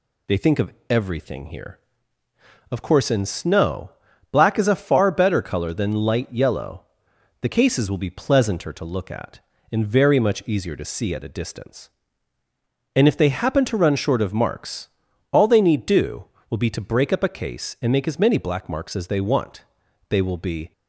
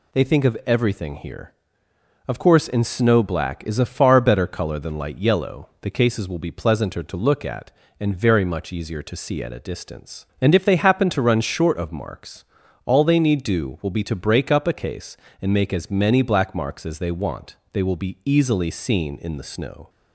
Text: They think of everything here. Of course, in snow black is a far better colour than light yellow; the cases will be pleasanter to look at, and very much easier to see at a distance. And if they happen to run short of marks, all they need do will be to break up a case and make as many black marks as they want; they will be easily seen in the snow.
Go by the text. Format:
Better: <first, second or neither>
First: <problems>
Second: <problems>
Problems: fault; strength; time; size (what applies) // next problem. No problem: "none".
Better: second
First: pauses between "of" and "everything"; slight; at 0.7 s; 0.18 s long // pauses between "snow" and "black"; at 3.9 s; 0.38 s long // stops before "easily seen in the snow"; at 20.7 s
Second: none